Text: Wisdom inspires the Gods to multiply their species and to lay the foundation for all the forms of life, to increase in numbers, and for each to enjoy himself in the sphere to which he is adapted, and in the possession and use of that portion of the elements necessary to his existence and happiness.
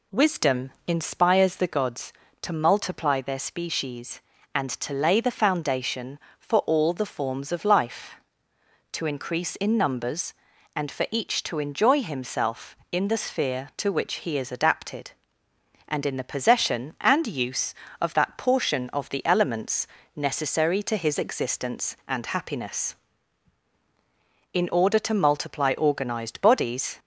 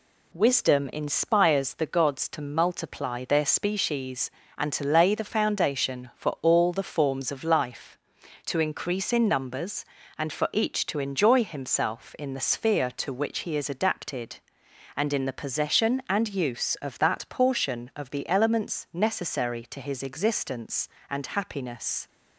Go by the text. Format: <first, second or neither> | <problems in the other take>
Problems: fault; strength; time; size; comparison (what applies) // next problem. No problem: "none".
second | pauses between "Wisdom" and "inspires"; slight; at 0.7 s; 0.16 s long // pauses between "elements" and "necessary"; slight; at 19.8 s; 0.30 s long // goes on to say "In order to multiply organized bodies"; strong; from 24.5 s on; 2.4 s long